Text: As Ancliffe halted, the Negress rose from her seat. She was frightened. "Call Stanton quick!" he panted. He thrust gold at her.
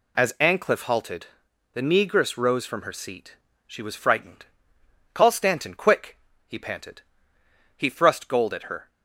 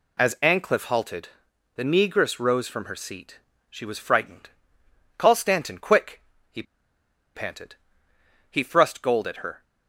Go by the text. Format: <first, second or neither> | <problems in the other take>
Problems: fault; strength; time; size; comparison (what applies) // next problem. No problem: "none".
first | pauses between "he" and "panted"; noticeable; at 6.6 s; 0.72 s long